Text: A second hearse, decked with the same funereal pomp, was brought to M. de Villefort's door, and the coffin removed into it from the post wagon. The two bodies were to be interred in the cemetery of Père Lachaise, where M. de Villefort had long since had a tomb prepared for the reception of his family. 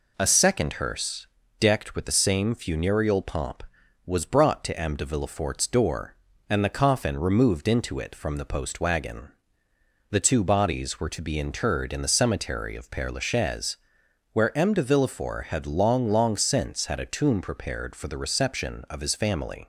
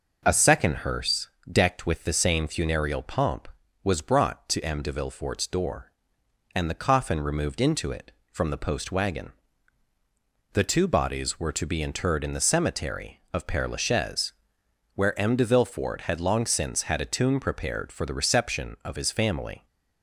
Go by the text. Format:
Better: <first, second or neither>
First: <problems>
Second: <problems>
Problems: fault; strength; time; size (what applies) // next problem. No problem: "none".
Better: second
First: says "long" twice; at 16.0 s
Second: none